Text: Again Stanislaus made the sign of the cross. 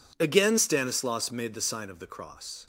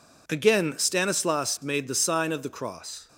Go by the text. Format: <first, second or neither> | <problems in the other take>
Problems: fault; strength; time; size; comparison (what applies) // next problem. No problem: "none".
neither | none